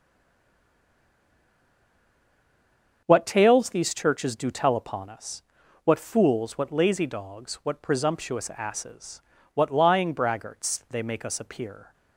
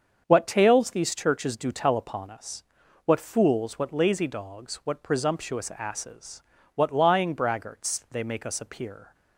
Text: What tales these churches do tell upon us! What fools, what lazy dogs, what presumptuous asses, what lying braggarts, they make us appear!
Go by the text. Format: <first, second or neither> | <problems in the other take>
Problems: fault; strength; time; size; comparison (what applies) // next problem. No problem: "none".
second | stays silent before the first word; strong; until 3.0 s; 3.0 s long // starts louder than the rest; until 4.0 s; 6.5 dB; also in the second